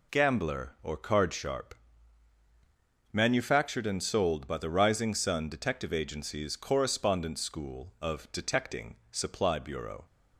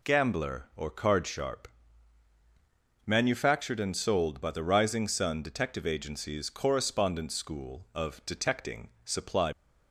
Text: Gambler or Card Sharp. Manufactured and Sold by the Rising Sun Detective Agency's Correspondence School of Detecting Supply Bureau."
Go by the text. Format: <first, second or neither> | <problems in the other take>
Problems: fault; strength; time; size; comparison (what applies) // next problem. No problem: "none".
first | pauses between "Detecting" and "Supply"; slight; at 8.8 s; 0.16 s long; slight in the first // stops before "Bureau"; at 9.5 s